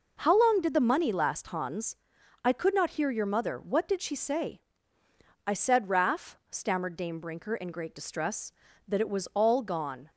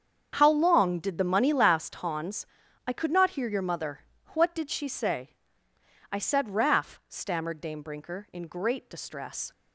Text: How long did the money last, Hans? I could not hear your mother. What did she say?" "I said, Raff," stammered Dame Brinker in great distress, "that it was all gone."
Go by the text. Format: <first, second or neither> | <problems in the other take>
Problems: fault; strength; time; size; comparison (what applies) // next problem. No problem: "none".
first | starts louder than the rest; strong; until 1.3 s; 7.5 dB // stops before "that it was all gone"; at 9.5 s